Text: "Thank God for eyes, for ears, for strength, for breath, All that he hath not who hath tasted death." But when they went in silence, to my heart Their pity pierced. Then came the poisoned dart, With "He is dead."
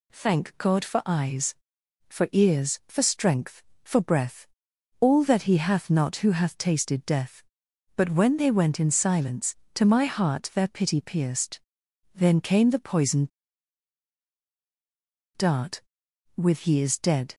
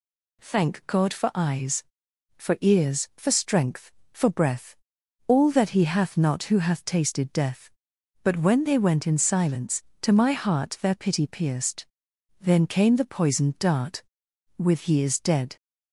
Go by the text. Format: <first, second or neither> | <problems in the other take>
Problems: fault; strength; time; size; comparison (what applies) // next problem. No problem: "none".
second | pauses between "poisoned" and "dart"; strong; at 13.2 s; 2.0 s long